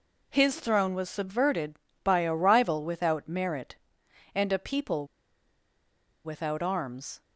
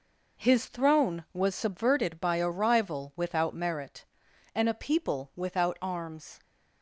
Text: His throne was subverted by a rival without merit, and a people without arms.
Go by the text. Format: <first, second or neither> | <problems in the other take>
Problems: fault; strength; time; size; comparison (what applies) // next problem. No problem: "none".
second | pauses between "people" and "without"; at 5.0 s; 1.1 s long